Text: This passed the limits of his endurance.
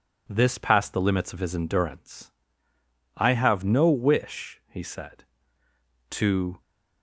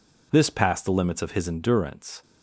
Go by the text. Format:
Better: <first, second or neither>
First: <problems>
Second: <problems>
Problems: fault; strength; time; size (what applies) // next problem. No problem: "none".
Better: second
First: goes on to say "I have no wish he said to"; strong; from 3.1 s on; 3.4 s long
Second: none